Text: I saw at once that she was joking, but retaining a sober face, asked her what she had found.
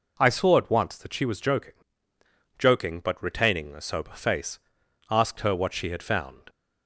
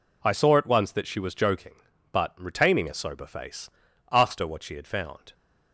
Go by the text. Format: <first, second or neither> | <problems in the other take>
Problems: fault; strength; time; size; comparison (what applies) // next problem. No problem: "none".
second | says "joking" twice; at 2.5 s